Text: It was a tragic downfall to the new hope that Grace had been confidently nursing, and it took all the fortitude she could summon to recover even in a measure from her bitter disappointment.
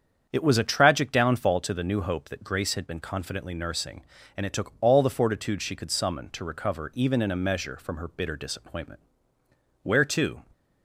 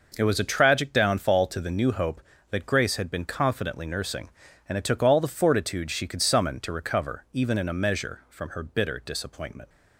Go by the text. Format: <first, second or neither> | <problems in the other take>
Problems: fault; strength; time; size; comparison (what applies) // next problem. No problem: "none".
second | starts louder than the rest; strong; until 1.3 s; 8 dB // goes on to say "Where to"; from 9.8 s on; 0.58 s long